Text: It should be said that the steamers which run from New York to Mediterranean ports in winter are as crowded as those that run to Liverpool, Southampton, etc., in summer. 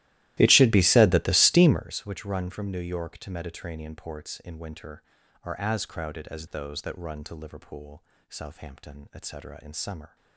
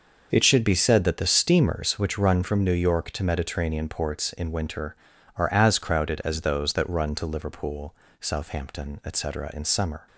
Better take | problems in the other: second | starts louder than the rest; strong; until 1.8 s; 16 dB

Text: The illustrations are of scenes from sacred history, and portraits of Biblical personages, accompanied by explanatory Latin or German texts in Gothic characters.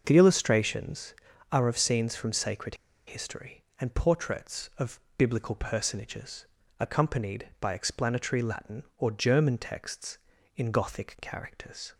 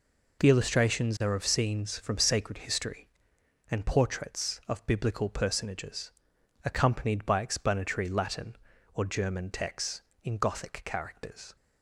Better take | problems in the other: second | starts louder than the rest; noticeable; until 1.0 s; 6 dB // pauses between "sacred" and "history"; slight; at 2.7 s; 0.31 s long // pauses between "of" and "Biblical"; slight; at 4.9 s; 0.16 s long

